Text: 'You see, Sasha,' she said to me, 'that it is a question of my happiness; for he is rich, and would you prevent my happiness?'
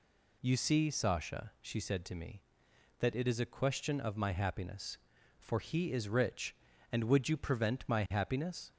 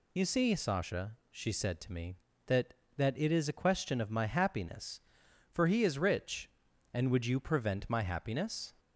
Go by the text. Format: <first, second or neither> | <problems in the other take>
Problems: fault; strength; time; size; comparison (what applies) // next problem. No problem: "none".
first | says "that" twice; at 2.9 s